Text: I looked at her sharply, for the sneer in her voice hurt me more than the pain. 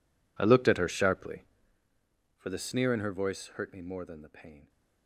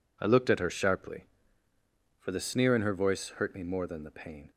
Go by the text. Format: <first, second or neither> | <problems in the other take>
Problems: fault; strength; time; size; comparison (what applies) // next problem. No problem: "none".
second | gets quieter; strong; throughout; 20.5 dB